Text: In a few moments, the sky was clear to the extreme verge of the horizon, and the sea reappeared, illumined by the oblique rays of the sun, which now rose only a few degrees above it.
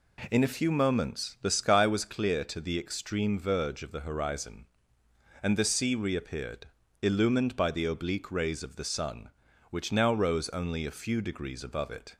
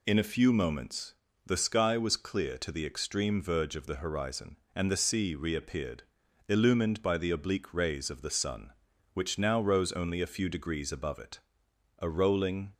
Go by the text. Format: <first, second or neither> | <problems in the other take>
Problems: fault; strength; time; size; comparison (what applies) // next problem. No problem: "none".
first | goes on to say "A rolling"; noticeable; from 11.9 s on; 0.76 s long